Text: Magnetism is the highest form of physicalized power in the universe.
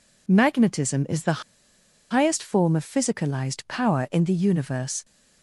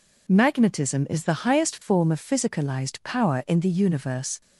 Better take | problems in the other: second | pauses between "the" and "highest"; noticeable; at 1.4 s; 0.70 s long

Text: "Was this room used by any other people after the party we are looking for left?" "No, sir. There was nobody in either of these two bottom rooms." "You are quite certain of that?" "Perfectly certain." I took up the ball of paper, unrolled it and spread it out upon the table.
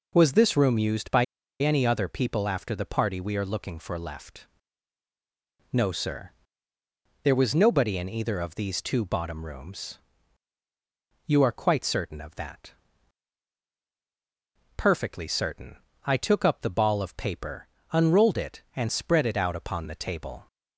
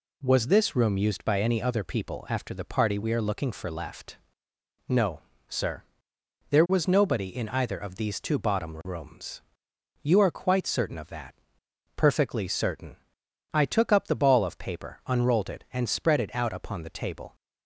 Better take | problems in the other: second | pauses between "by" and "any"; at 1.2 s; 0.36 s long

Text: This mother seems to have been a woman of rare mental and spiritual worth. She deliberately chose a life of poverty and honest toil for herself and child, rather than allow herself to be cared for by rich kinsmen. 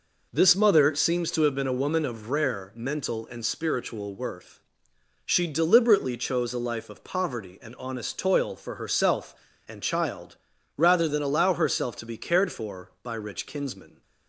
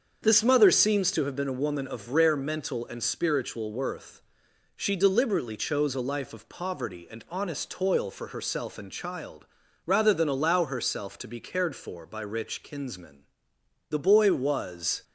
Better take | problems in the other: first | starts louder than the rest; until 1.2 s; 7 dB // goes on to say "The boy was"; noticeable; from 13.8 s on; 1.1 s long

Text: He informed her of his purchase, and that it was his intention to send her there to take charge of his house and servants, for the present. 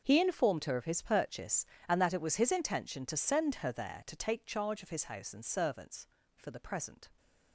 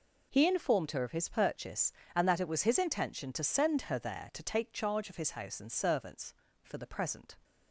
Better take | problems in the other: second | gets quieter; strong; throughout; 16 dB

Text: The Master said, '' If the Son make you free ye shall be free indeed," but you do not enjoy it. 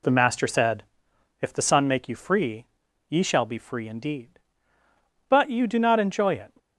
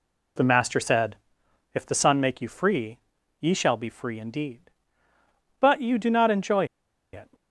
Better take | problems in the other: first | pauses between "free" and "ye"; at 2.9 s; 0.42 s long; also in the first // pauses between "enjoy" and "it"; noticeable; at 6.6 s; 0.48 s long

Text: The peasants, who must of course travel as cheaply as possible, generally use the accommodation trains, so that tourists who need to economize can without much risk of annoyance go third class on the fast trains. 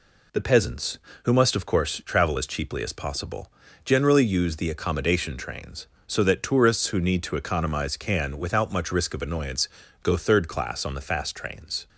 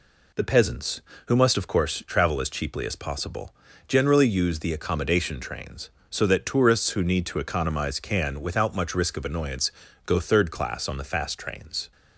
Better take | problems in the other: neither | pauses between "annoyance" and "go"; slight; the same in both

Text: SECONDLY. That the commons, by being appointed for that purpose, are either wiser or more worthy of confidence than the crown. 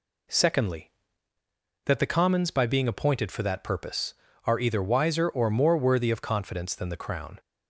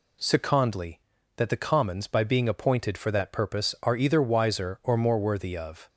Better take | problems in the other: first | stops before "confidence than the crown"; at 5.8 s

